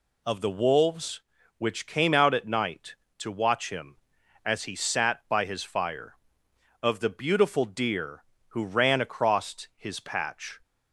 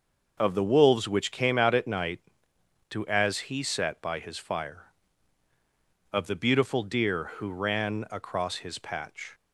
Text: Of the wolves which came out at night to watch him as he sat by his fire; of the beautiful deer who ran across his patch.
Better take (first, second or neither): first